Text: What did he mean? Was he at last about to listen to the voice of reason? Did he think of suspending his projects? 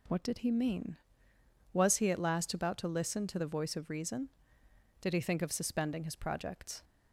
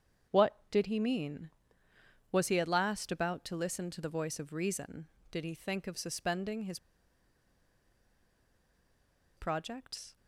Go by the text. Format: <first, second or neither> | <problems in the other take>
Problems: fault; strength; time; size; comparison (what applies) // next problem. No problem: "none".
first | starts louder than the rest; strong; until 1.4 s; 8 dB // pauses between "his" and "projects"; strong; at 6.7 s; 2.5 s long